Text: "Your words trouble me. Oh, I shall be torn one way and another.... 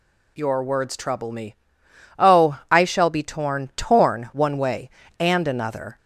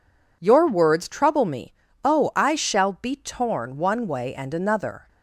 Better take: second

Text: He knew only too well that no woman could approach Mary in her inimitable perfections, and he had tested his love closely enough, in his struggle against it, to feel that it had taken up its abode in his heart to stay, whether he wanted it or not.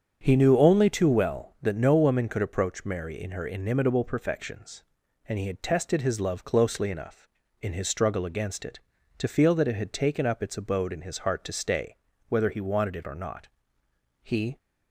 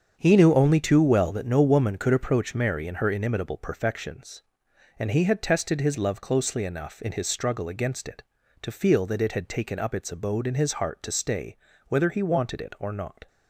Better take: second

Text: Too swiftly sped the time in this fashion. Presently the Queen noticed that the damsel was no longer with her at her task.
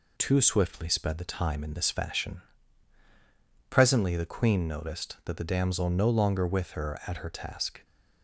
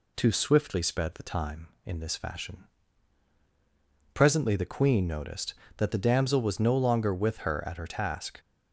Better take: second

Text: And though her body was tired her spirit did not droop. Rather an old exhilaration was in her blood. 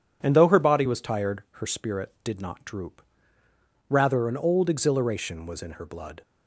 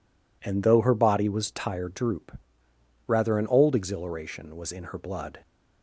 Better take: first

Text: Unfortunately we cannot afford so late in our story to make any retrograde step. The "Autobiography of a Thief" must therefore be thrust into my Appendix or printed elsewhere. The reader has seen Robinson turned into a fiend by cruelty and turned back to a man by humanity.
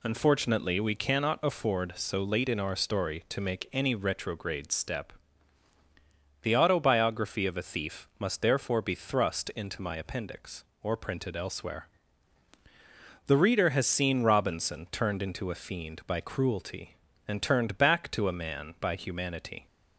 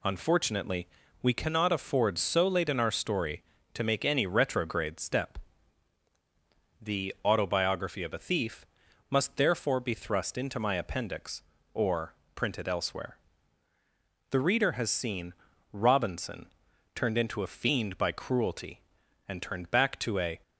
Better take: first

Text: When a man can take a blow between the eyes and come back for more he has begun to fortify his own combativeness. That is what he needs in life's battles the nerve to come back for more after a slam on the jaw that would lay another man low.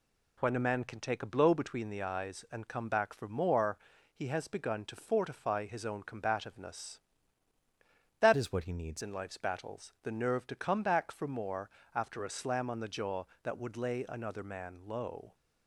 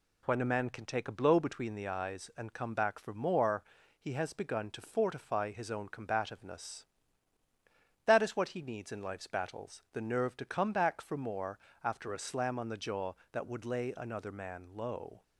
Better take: second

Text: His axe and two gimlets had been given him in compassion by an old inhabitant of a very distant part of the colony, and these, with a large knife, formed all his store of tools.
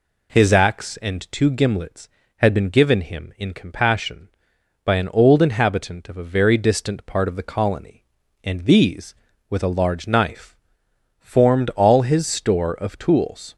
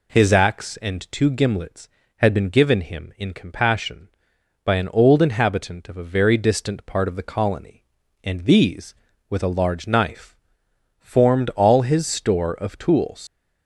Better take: first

